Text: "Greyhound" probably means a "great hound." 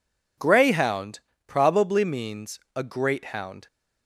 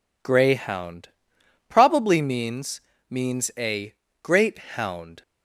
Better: first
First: pauses between "Greyhound" and "probably"; slight; at 1.1 s; 0.28 s long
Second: pauses between "Greyhound" and "probably"; noticeable; at 1.0 s; 0.62 s long // says "means" twice; at 3.0 s // pauses between "a" and "great"; slight; at 3.9 s; 0.28 s long

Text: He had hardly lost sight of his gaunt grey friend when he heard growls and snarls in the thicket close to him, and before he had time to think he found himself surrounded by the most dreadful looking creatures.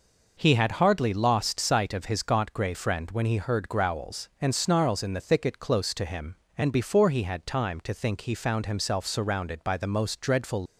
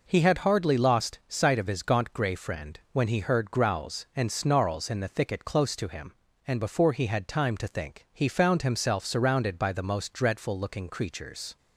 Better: second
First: stops before "looking creatures"; at 10.6 s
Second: none

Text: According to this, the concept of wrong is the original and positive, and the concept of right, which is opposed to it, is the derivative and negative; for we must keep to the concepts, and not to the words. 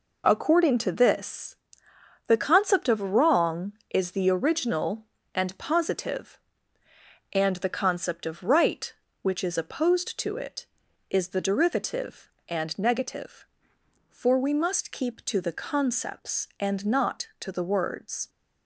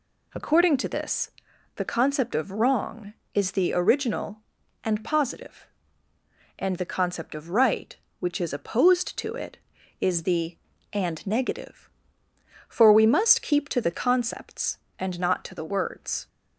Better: first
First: none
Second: skips "derivative"; at 10.7 s

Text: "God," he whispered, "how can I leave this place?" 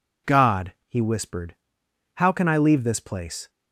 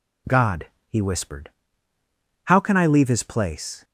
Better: first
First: none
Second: says "his" for "this"; at 3.0 s

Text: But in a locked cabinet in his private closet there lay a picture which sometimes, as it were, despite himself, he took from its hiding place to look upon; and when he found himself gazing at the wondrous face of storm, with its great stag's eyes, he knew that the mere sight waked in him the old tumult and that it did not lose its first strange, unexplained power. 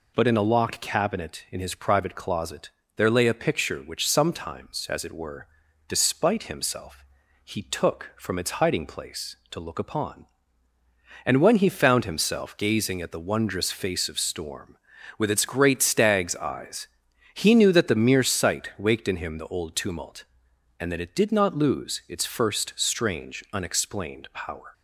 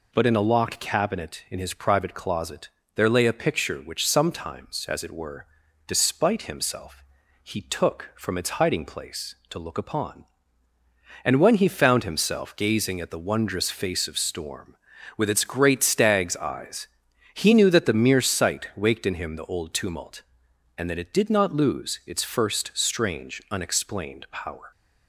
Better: neither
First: pauses between "closet" and "there"; slight; at 2.6 s; 0.28 s long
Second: pauses between "closet" and "there"; slight; at 2.6 s; 0.28 s long

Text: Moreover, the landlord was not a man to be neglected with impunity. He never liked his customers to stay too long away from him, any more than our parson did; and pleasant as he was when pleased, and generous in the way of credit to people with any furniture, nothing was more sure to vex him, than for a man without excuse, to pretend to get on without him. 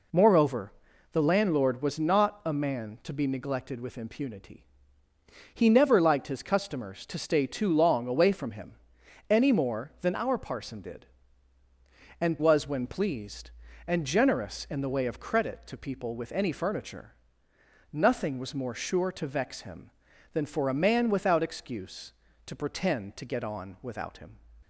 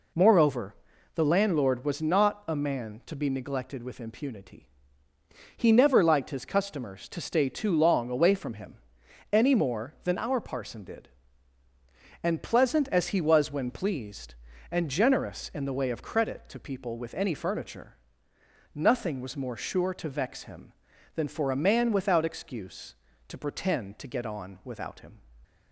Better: second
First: skips "pleasant as he"; at 12.3 s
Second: none

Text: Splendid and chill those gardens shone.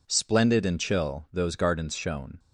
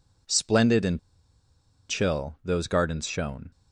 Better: first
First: none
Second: pauses between "and" and "chill"; noticeable; at 0.9 s; 0.90 s long

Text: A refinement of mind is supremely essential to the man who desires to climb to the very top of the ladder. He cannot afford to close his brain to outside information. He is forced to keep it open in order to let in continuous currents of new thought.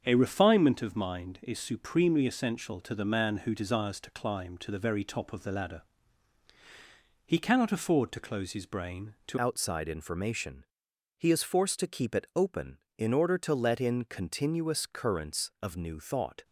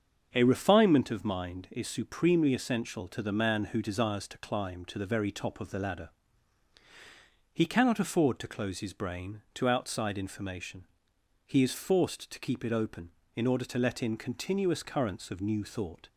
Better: second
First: starts louder than the rest; until 1.0 s; 7 dB // changes voice at "outside"; from 9.3 s on; 7.1 s long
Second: starts louder than the rest; until 1.3 s; 7 dB

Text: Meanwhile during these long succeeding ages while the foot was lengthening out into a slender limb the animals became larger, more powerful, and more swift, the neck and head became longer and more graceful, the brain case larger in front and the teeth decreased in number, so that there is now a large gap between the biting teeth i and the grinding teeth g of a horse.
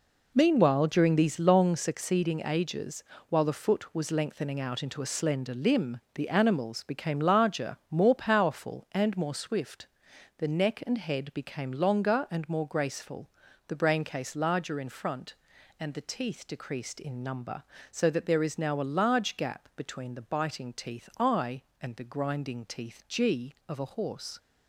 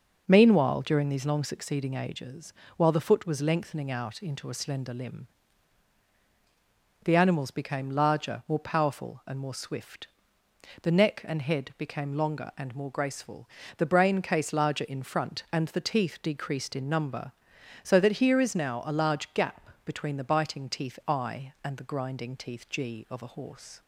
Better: first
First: pauses between "ages" and "while"; slight; at 3.0 s; 0.26 s long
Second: pauses between "ages" and "while"; slight; at 2.5 s; 0.26 s long // pauses between "limb" and "the"; strong; at 5.2 s; 1.7 s long // says "here" for "there"; at 18.1 s // pauses between "gap" and "between"; slight; at 19.6 s; 0.16 s long

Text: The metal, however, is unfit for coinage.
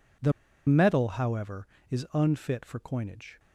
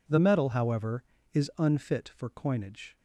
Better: second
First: pauses between "The" and "metal"; slight; at 0.3 s; 0.35 s long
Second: none

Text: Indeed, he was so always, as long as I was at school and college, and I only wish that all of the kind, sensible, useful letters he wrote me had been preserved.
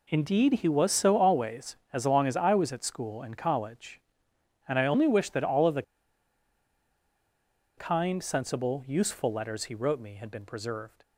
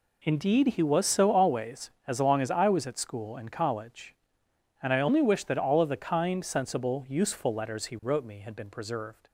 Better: second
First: pauses between "the" and "kind"; strong; at 5.8 s; 1.9 s long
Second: none

